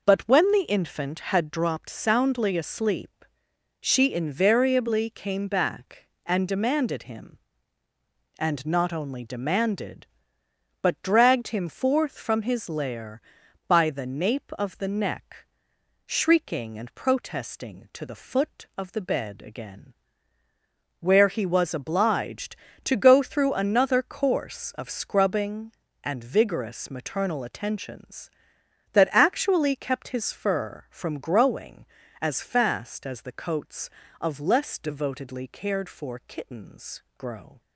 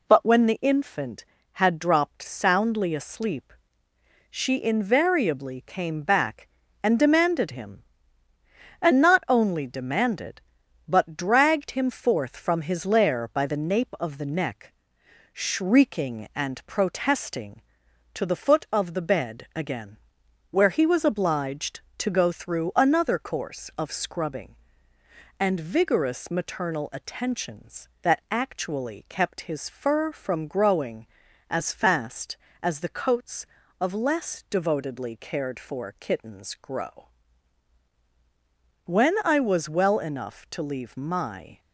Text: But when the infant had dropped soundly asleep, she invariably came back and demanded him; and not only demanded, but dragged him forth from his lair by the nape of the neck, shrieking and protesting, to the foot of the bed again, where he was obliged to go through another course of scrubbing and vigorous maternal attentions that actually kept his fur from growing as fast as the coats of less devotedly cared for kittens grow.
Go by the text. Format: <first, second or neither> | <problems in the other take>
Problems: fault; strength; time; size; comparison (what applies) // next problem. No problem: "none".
first | goes on to say "When I was well enough to leave my"; strong; from 38.8 s on; 2.7 s long